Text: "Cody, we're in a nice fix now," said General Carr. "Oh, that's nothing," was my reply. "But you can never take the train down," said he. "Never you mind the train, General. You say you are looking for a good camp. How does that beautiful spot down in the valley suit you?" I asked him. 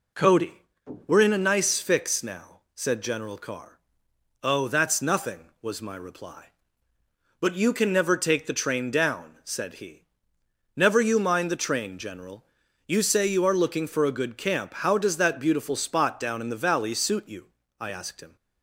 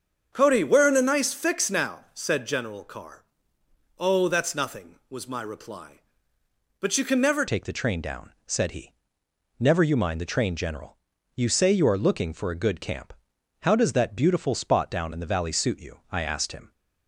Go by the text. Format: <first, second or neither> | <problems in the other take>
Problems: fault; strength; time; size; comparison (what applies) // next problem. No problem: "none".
first | starts louder than the rest; strong; until 1.3 s; 7.5 dB // changes voice at "take"; from 7.4 s on; 9.3 s long